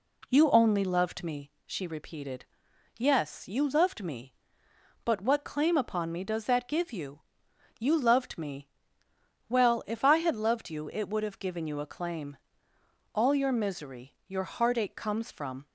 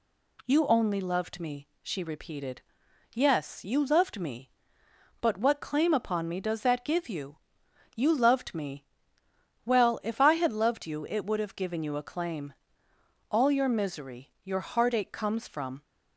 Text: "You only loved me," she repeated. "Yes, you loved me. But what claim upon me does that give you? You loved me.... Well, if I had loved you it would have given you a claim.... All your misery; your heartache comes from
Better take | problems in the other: second | starts louder than the rest; slight; until 1.4 s; 2 dB

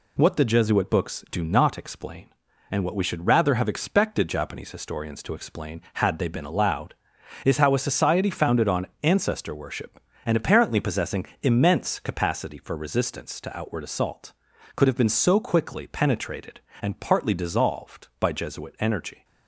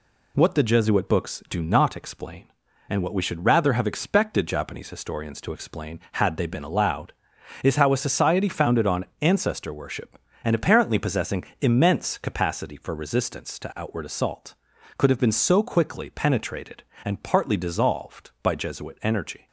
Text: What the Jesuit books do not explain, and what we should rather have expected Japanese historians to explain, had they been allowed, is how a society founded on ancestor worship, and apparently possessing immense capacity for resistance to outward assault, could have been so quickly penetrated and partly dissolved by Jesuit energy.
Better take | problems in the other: neither | pauses between "on" and "ancestor"; slight; the same in both // pauses between "possessing" and "immense"; slight; the same in both

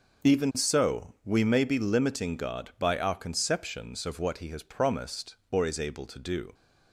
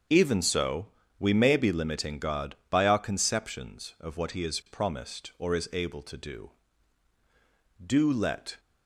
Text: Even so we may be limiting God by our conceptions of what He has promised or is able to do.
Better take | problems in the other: first | starts louder than the rest; until 1.4 s; 7 dB // pauses between "so" and "we"; slight; at 0.8 s; 0.32 s long // goes on to say "Do let"; noticeable; from 7.8 s on; 0.74 s long

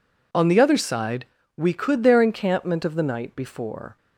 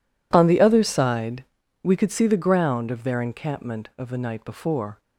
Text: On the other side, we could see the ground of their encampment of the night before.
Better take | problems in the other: second | skips "see the ground of"; at 2.0 s

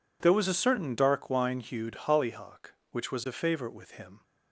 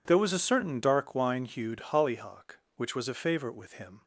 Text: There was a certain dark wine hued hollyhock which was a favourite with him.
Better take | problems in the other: neither | none

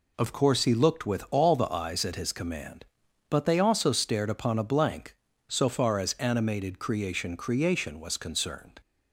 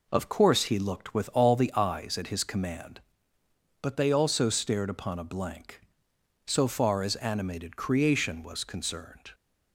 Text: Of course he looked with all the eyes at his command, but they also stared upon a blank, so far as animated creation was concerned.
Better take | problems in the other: second | says "creation" twice; at 7.3 s

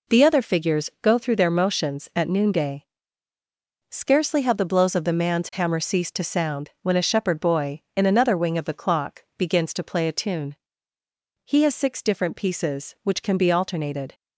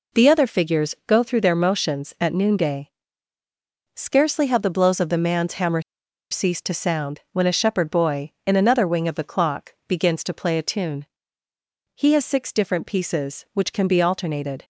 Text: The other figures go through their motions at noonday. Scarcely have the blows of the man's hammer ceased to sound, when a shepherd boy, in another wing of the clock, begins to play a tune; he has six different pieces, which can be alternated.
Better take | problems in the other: first | pauses between "hammer" and "ceased"; noticeable; at 5.8 s; 0.48 s long

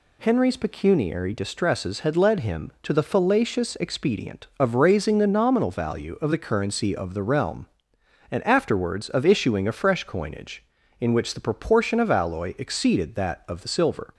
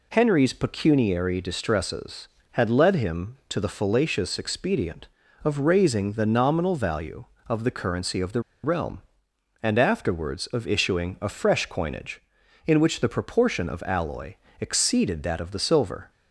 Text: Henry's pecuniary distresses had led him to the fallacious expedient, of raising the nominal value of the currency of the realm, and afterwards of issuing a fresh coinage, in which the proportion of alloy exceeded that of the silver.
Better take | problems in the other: first | pauses between "the" and "realm"; slight; at 8.4 s; 0.22 s long // pauses between "alloy" and "exceeded"; slight; at 14.3 s; 0.26 s long

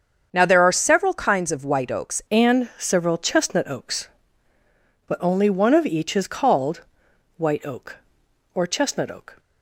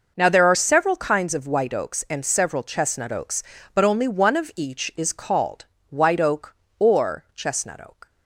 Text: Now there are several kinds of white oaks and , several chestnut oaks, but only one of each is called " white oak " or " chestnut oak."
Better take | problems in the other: second | starts louder than the rest; strong; until 1.3 s; 7.5 dB // changes voice at "and"; from 2.2 s on; 7.1 s long

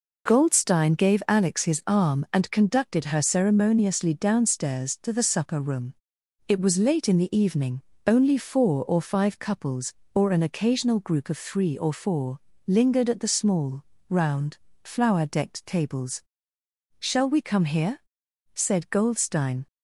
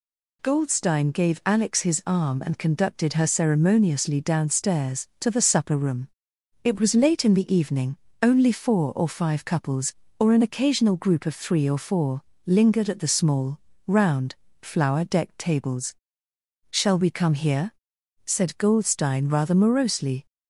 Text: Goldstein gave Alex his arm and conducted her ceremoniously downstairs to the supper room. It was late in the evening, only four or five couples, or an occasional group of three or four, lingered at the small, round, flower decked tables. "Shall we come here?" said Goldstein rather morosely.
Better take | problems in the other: second | stops before "rather morosely"; at 19.6 s

